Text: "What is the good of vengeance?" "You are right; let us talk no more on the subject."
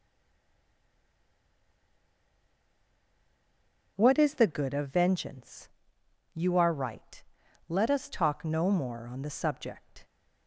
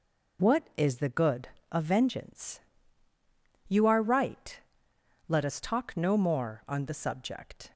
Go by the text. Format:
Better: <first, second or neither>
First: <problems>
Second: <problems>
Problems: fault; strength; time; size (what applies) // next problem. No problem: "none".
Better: second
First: stays silent before the first word; strong; until 3.9 s; 3.9 s long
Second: none